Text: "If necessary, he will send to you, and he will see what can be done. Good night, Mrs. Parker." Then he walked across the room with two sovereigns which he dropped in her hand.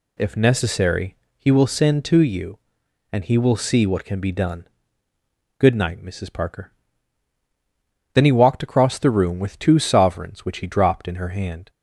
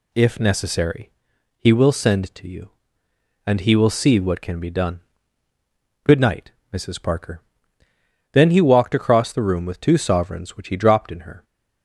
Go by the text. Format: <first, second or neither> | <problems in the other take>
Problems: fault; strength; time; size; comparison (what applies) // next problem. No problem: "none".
first | stops before "hand"; at 11.4 s